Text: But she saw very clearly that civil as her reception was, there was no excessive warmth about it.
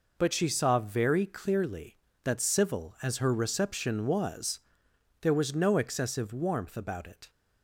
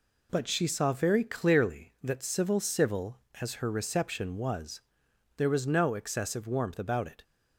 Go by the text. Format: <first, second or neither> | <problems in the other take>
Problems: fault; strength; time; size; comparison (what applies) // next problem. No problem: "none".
first | says "civil" twice; at 2.6 s